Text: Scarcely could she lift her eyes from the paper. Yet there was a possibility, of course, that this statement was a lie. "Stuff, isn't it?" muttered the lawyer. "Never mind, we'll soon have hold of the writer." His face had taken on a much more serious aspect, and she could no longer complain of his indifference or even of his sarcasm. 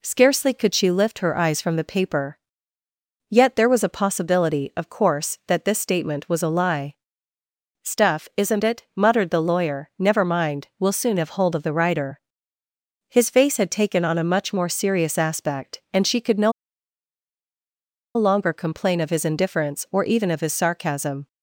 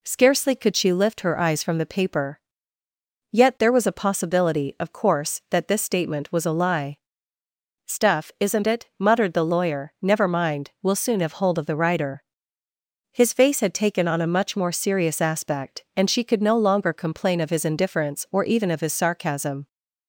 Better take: second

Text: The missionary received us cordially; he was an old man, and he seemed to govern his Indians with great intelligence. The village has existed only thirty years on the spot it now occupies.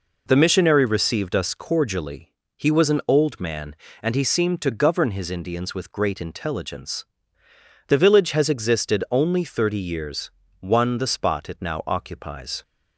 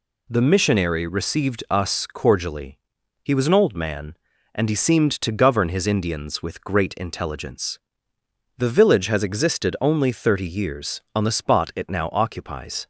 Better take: second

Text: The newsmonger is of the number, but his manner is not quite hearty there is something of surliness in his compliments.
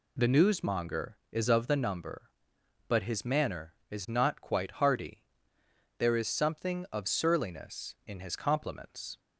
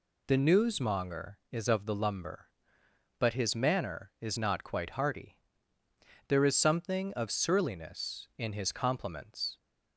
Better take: first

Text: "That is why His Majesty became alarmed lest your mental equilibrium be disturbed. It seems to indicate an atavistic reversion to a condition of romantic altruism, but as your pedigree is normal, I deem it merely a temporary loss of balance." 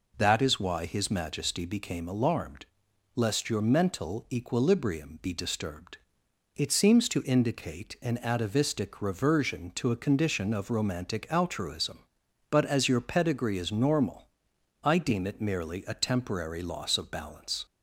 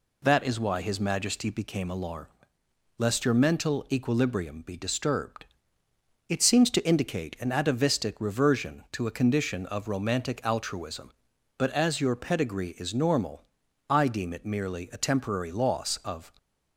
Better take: first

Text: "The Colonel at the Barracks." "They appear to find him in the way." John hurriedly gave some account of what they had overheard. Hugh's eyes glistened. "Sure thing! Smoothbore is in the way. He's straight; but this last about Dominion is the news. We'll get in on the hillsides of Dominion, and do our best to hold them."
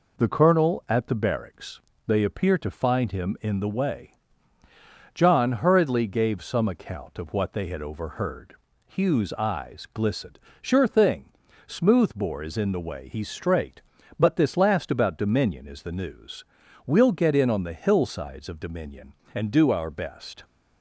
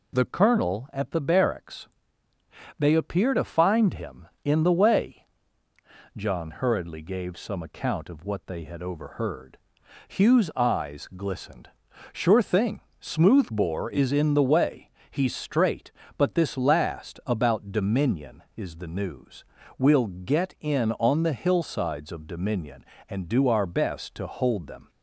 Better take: second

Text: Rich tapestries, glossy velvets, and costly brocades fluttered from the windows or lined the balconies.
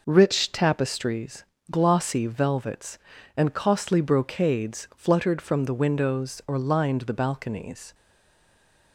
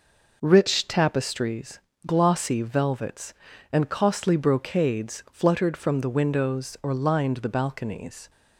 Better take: second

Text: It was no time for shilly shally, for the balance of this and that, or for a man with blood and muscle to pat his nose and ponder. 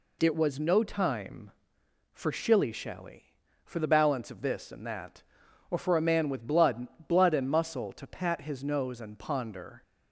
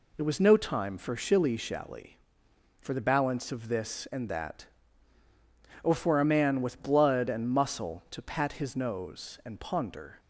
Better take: second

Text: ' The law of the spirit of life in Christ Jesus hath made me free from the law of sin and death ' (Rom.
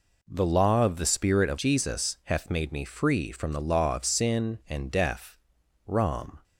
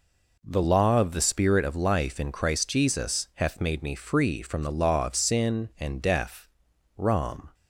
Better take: second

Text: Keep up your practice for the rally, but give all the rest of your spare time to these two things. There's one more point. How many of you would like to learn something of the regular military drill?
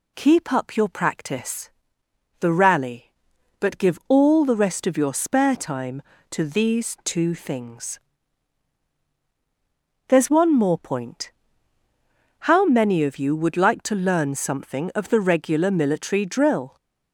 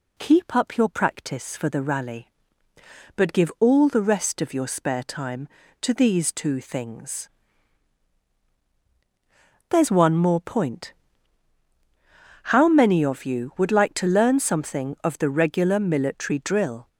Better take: second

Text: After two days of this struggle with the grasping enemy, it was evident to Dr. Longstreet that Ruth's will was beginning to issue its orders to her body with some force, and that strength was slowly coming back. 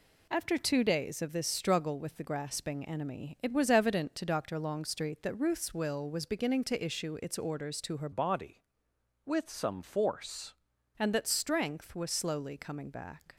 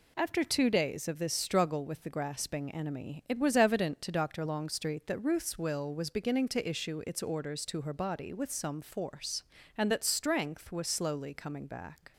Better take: second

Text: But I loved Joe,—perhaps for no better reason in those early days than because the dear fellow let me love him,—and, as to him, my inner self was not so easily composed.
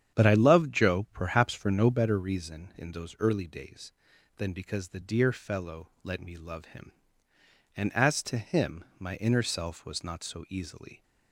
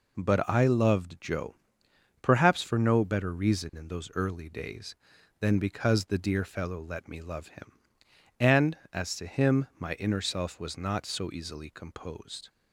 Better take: second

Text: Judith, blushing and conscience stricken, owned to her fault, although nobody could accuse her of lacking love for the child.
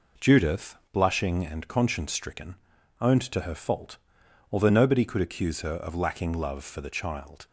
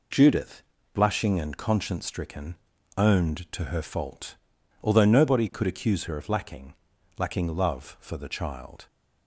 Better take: first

